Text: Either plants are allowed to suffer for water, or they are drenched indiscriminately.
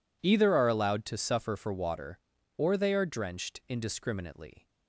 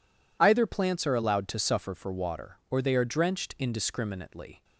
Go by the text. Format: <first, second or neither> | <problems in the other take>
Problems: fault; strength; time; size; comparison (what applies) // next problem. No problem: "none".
second | skips "plants"; at 0.5 s